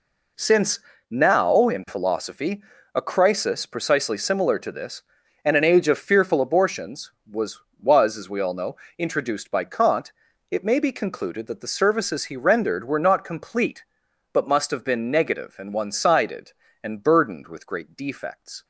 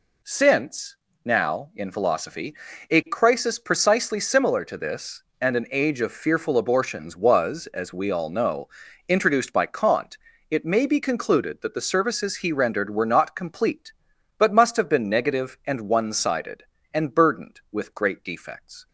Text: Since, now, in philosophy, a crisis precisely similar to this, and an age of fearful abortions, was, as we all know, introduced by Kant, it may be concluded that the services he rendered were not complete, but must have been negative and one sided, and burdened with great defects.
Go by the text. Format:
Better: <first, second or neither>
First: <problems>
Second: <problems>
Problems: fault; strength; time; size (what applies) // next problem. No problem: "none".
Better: second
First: says "was" twice; at 7.8 s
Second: none